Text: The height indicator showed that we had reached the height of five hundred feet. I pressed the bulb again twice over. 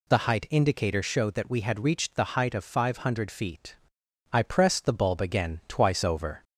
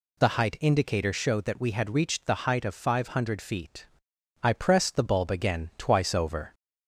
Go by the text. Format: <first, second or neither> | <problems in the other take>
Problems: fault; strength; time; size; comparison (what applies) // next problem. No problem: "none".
neither | none